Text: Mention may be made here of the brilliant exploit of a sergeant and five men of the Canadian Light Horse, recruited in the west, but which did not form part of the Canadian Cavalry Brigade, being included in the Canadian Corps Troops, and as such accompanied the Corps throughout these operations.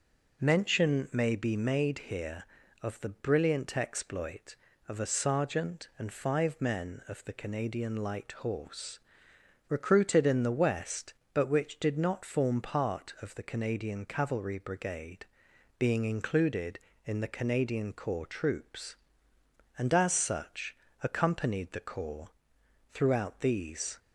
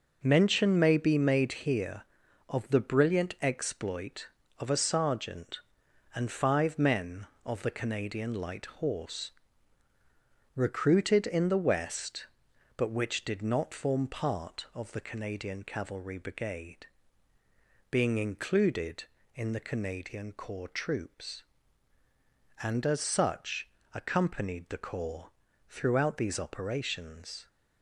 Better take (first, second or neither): second